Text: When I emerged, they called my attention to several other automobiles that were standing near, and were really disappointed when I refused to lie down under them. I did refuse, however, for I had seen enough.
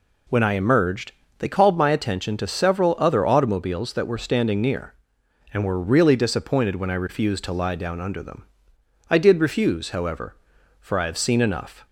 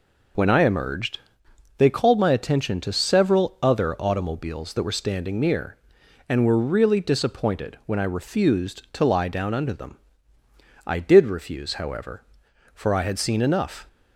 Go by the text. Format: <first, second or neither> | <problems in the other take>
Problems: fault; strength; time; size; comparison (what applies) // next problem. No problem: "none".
second | says "have" for "had"; at 11.0 s